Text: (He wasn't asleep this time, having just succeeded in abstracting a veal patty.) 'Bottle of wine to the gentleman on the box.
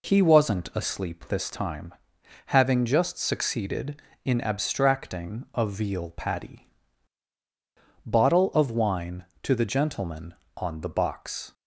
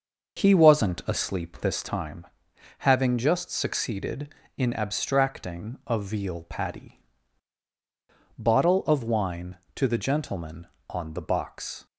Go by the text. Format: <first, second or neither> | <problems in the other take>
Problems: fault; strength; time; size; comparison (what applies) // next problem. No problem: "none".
first | starts louder than the rest; noticeable; until 2.0 s; 6 dB